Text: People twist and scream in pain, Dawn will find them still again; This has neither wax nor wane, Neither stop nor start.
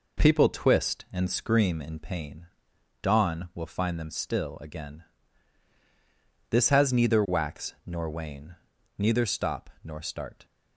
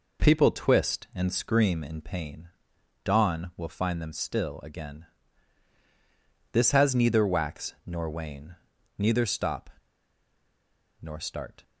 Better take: first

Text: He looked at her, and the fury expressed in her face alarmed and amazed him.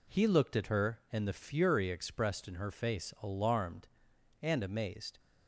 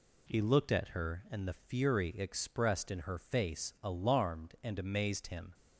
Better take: second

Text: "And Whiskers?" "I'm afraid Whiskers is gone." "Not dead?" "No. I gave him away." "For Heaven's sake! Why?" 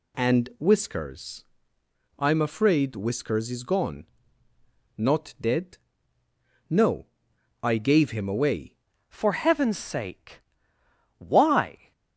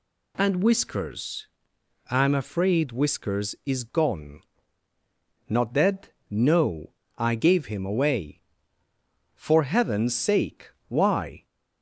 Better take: second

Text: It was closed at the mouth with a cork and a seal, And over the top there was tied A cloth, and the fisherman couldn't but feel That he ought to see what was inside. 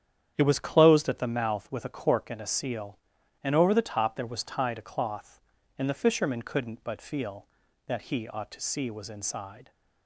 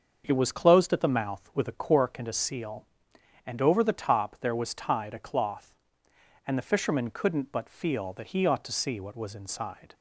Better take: second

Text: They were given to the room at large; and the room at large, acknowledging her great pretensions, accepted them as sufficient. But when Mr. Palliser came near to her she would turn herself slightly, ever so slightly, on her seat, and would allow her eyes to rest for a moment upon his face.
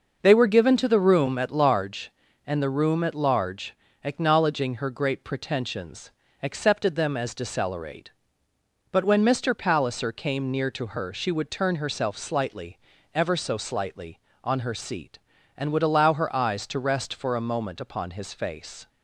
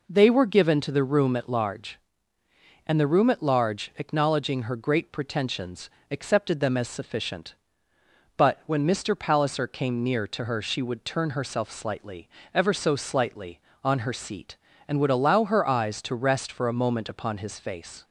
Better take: second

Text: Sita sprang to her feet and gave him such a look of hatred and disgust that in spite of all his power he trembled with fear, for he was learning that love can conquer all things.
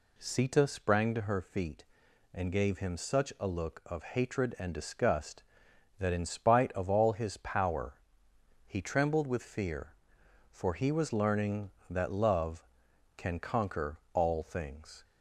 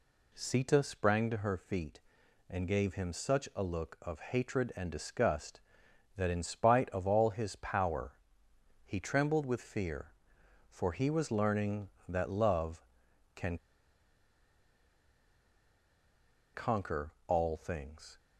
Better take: first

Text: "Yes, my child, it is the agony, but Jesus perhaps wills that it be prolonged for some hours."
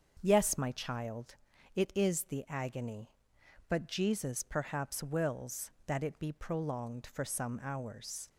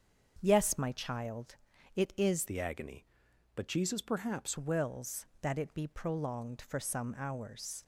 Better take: first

